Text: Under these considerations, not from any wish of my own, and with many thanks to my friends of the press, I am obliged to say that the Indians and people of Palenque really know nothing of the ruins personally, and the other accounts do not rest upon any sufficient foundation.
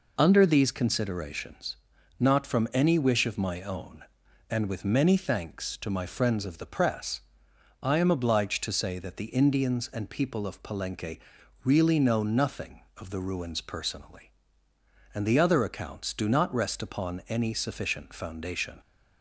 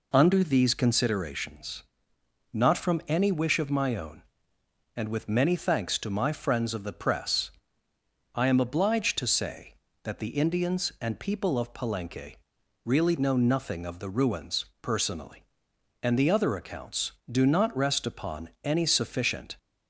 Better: first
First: pauses between "Palenque" and "really"; noticeable; at 11.1 s; 0.46 s long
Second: pauses between "Palenque" and "really"; noticeable; at 12.3 s; 0.48 s long // pauses between "ruins" and "personally"; slight; at 14.6 s; 0.16 s long // stops before "foundation"; at 19.5 s

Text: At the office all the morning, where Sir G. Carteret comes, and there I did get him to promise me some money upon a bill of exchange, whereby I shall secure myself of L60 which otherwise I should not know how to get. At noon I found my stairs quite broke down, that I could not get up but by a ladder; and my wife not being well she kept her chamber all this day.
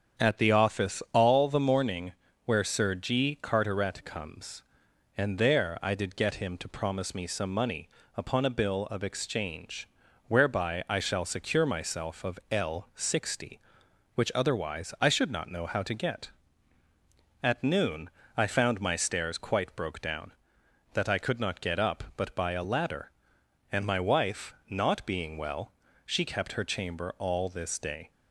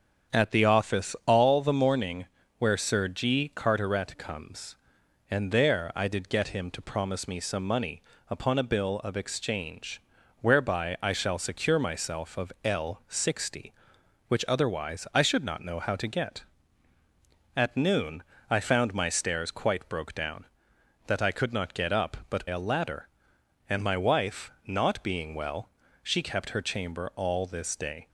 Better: first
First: starts louder than the rest; strong; until 1.2 s; 7.5 dB // pauses between "money" and "upon"; slight; at 7.8 s; 0.28 s long // pauses between "noon" and "I"; slight; at 18.0 s; 0.26 s long // pauses between "wife" and "not"; slight; at 24.5 s; 0.16 s long // pauses between "well" and "she"; slight; at 25.7 s; 0.32 s long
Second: starts louder than the rest; strong; until 1.4 s; 7.5 dB // pauses between "money" and "upon"; slight; at 7.9 s; 0.28 s long // pauses between "noon" and "I"; slight; at 18.2 s; 0.26 s long // skips "by"; at 22.4 s // pauses between "wife" and "not"; slight; at 24.5 s; 0.16 s long // pauses between "well" and "she"; slight; at 25.7 s; 0.32 s long

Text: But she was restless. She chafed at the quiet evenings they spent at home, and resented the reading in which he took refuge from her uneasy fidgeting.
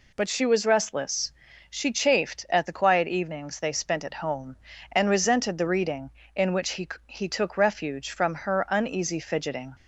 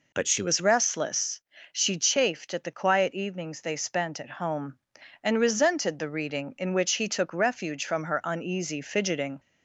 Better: second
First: says "he" twice; at 7.0 s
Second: none

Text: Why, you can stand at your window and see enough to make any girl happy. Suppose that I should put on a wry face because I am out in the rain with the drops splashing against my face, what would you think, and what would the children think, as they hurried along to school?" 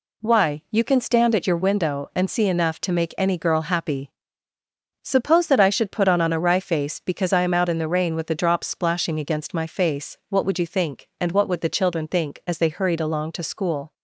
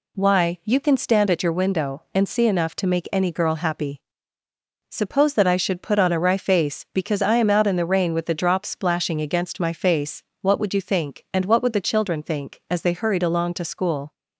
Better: second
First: says "on" twice; at 6.2 s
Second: none

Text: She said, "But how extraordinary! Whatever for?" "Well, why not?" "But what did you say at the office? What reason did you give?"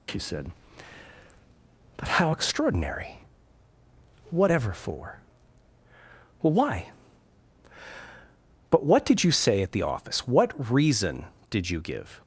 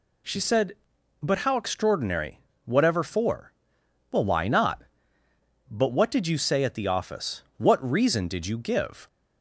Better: second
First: skips "not"; at 7.8 s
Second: none

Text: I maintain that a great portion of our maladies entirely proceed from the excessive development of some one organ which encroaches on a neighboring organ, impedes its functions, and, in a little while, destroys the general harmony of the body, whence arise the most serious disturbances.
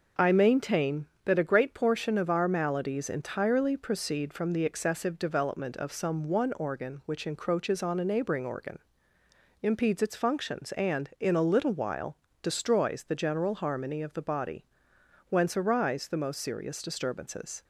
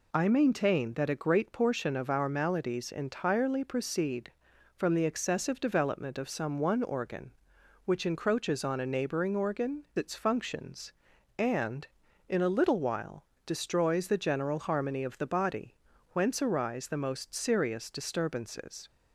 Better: first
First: none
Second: skips "impedes"; at 9.9 s

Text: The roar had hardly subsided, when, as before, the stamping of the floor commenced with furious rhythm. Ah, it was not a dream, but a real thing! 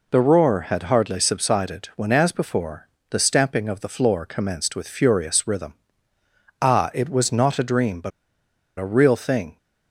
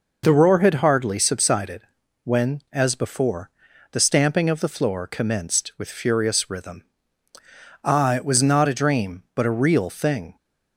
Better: second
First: pauses between "but" and "a"; noticeable; at 8.1 s; 0.68 s long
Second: none

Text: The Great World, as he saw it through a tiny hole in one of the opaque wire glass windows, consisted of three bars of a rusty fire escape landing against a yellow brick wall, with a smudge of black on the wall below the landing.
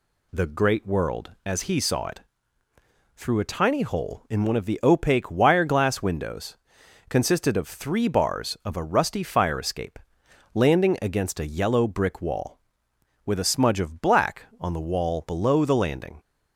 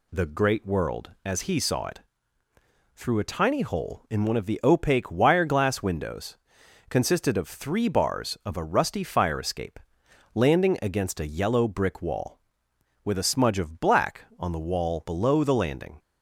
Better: neither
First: pauses between "it" and "through"; noticeable; at 2.2 s; 0.94 s long // pauses between "escape" and "landing"; noticeable; at 9.9 s; 0.56 s long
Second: pauses between "it" and "through"; noticeable; at 2.0 s; 0.94 s long // pauses between "escape" and "landing"; noticeable; at 9.7 s; 0.56 s long

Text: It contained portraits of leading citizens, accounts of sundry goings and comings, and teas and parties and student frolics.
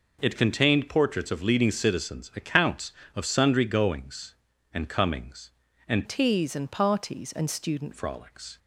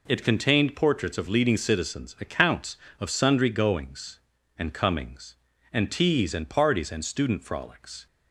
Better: second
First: changes voice from "teas" to "student"; from 6.0 to 7.9 s; 1.9 s long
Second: none

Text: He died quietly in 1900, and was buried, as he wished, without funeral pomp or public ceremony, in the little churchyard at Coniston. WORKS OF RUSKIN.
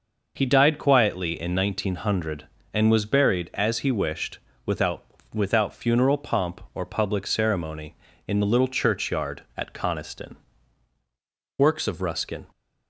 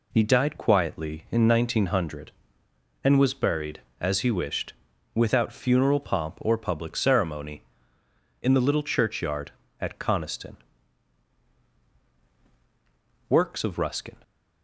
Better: second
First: says "without" twice; at 5.3 s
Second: none

